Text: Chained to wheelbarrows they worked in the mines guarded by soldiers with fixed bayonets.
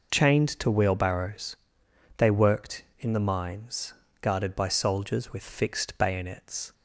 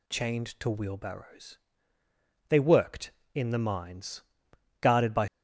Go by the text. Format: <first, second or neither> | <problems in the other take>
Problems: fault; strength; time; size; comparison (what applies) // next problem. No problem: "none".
first | pauses between "wheelbarrows" and "they"; noticeable; at 1.5 s; 0.92 s long; noticeable in the first // pauses between "mines" and "guarded"; noticeable; at 4.2 s; 0.58 s long; slight in the first // stops before "soldiers with fixed bayonets"; at 5.2 s